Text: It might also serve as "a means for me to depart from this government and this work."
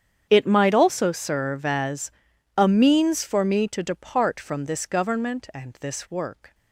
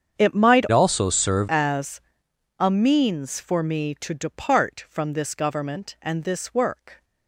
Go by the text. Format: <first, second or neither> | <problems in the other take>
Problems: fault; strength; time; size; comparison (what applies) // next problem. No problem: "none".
first | starts louder than the rest; strong; until 1.2 s; 8 dB; strong in the first // changes voice from "also" to "serve"; from 0.7 to 1.4 s; 0.7 s long // pauses between "as" and "a"; noticeable; at 2.0 s; 0.58 s long; noticeable in the first